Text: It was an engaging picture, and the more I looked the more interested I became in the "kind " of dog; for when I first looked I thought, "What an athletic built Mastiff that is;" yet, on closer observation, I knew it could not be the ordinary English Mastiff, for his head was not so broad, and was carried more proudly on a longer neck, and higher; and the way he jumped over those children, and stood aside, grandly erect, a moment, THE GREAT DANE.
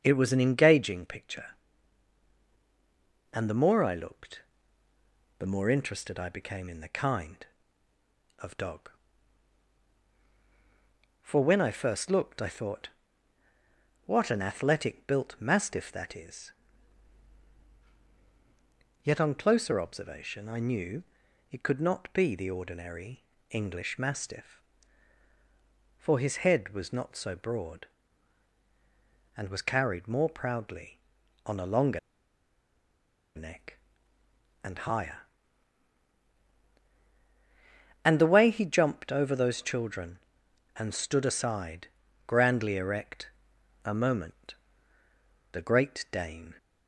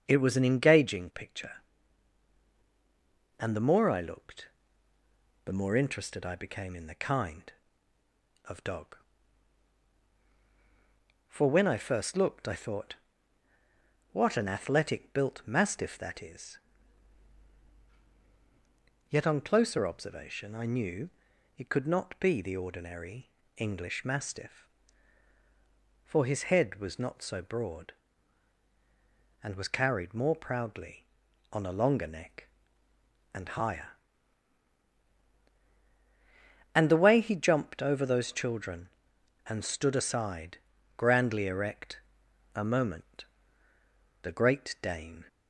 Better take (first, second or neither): second